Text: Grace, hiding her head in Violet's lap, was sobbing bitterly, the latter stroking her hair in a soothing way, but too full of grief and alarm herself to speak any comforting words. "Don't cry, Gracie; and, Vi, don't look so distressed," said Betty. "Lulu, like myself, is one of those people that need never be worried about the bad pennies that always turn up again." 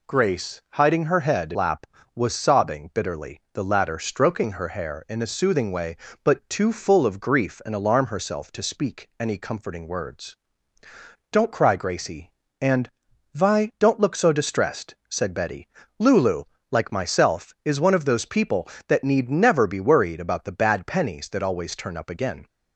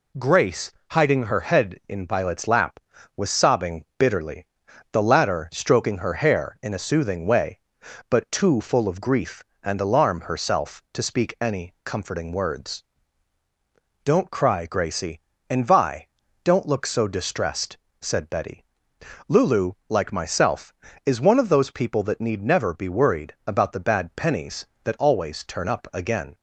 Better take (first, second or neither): second